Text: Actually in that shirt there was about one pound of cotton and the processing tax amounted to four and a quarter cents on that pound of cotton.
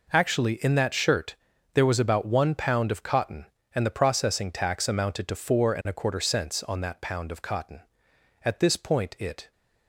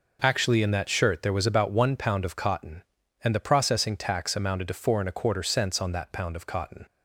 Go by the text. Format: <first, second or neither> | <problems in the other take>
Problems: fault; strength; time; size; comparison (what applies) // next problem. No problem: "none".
second | pauses between "shirt" and "there"; at 1.3 s; 0.40 s long // goes on to say "At this point it"; noticeable; from 8.4 s on; 1.0 s long